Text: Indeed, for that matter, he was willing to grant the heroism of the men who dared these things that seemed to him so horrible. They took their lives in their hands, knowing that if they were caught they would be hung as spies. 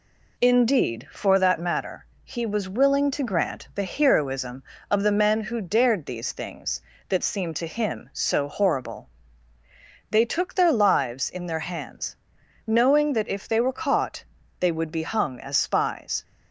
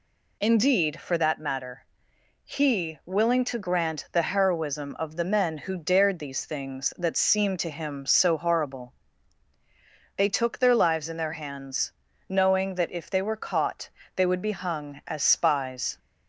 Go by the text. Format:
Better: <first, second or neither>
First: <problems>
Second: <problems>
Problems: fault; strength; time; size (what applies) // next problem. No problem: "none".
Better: first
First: pauses between "caught" and "they"; slight; at 14.2 s; 0.36 s long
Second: skips "was"; at 3.0 s // pauses between "caught" and "they"; slight; at 13.9 s; 0.26 s long